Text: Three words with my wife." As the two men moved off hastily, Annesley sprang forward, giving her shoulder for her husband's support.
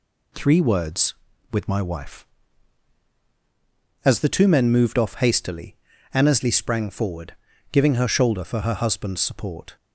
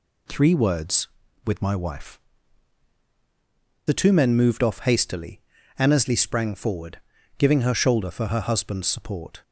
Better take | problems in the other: first | skips "As"; at 3.0 s

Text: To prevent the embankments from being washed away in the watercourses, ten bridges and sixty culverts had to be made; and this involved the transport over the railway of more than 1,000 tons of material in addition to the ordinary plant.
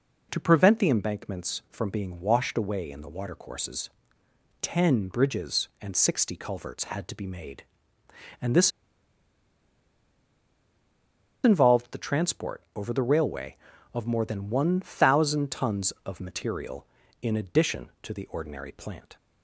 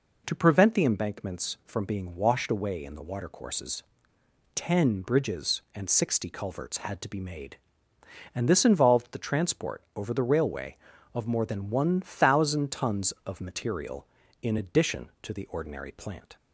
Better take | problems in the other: second | pauses between "this" and "involved"; strong; at 8.7 s; 2.7 s long

